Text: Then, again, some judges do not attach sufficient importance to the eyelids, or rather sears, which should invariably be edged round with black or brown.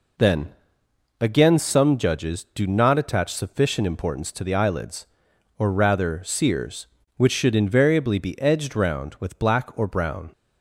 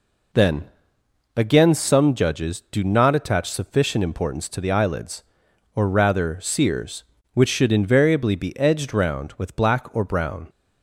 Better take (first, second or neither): neither